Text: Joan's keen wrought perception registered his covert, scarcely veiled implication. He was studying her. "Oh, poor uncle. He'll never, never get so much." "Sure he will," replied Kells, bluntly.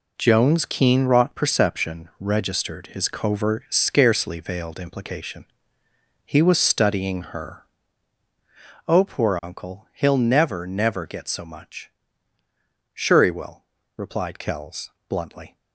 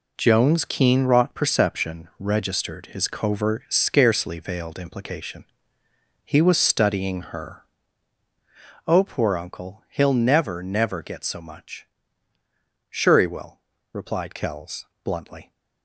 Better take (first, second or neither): neither